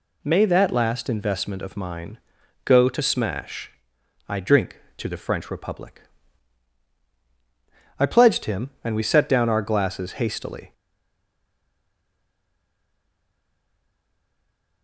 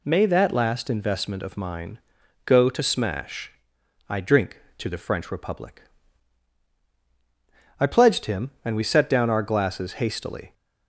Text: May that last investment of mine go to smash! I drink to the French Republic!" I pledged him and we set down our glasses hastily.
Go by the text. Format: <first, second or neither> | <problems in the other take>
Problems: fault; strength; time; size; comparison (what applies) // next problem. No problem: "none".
second | pauses between "mine" and "go"; noticeable; at 2.1 s; 0.46 s long; noticeable in the second // stays silent after the last word; strong; from 10.7 s on; 4.1 s long